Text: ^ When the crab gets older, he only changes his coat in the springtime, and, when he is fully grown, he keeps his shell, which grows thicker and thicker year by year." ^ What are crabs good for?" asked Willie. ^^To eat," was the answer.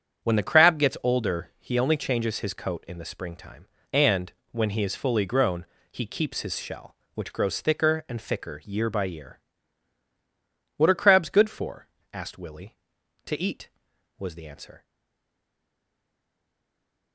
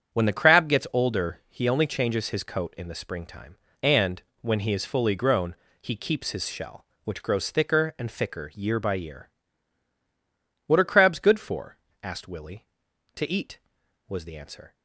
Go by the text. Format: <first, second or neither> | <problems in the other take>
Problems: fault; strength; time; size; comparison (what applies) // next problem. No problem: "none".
second | starts louder than the rest; strong; until 1.3 s; 8 dB; strong in the second // stays silent after the last word; from 14.8 s on; 2.3 s long